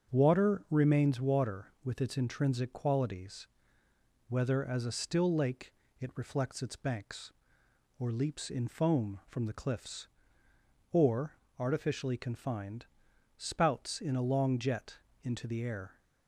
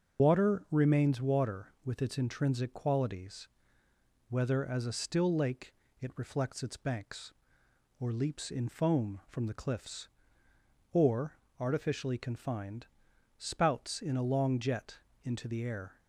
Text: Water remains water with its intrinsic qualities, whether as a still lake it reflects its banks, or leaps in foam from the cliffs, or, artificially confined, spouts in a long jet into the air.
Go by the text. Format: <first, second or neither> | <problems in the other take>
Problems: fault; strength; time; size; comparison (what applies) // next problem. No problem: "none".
first | loses the start of "Water"; at 0.1 s; 105 ms // starts louder than the rest; until 1.2 s; 6.5 dB; also in the first // pauses between "lake" and "it"; slight; at 5.7 s; 0.28 s long; slight in the first // pauses between "jet" and "into"; slight; at 14.9 s; 0.24 s long; slight in the first